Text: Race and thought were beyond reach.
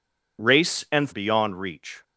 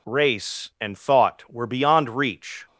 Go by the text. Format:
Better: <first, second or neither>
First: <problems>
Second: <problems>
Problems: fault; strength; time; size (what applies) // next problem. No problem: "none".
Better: second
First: skips "thought were"; at 1.1 s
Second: none